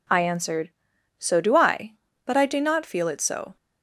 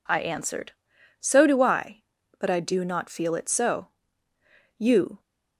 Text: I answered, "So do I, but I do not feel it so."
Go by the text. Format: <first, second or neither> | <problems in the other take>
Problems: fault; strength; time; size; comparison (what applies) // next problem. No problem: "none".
first | goes on to say "You"; slight; from 4.7 s on; 0.40 s long